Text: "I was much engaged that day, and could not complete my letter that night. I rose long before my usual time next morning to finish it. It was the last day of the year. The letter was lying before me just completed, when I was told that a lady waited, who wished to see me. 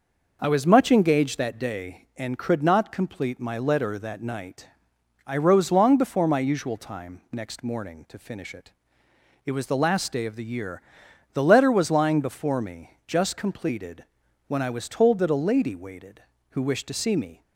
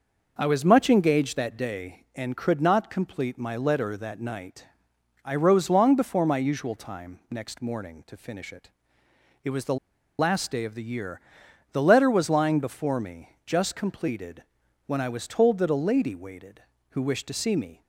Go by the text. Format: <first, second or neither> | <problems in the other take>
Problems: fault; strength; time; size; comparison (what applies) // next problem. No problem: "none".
first | pauses between "the" and "last"; at 9.7 s; 0.43 s long